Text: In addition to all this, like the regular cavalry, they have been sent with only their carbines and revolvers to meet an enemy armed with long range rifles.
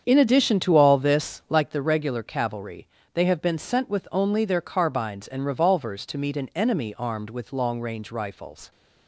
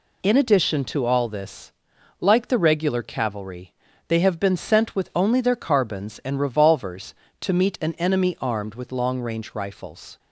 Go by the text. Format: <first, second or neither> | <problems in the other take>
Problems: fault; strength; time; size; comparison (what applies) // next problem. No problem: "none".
second | starts louder than the rest; strong; until 1.7 s; 7.5 dB